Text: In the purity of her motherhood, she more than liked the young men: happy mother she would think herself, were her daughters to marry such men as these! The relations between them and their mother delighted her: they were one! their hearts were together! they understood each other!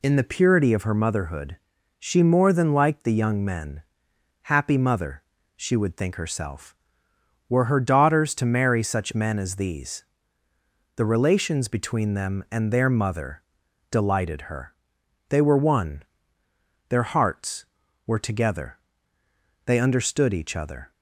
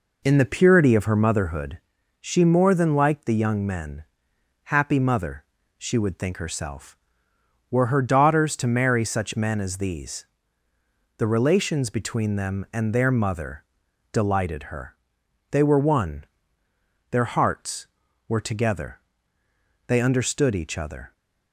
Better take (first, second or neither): first